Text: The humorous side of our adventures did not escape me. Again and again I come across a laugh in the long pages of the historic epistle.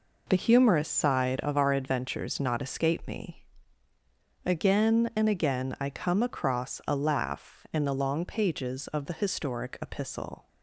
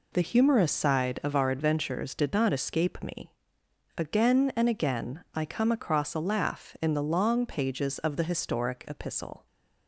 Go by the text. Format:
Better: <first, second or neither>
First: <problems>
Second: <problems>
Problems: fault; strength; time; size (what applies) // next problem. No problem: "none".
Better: second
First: skips "did"; at 2.3 s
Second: none